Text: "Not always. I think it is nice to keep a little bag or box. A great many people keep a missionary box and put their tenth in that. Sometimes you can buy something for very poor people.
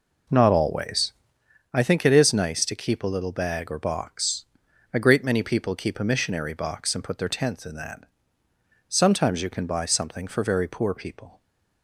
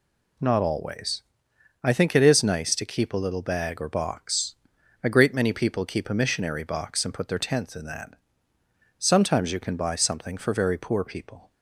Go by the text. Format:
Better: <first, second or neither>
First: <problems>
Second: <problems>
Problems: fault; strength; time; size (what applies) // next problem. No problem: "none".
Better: second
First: starts louder than the rest; noticeable; until 1.5 s; 4.5 dB // stays silent after the last word; slight; from 11.3 s on; 0.5 s long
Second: none